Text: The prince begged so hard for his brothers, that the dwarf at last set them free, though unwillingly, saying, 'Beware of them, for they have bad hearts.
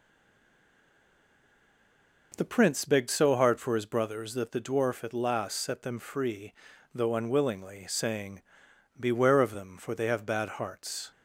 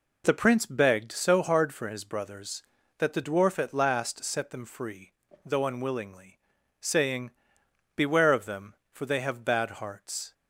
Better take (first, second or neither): second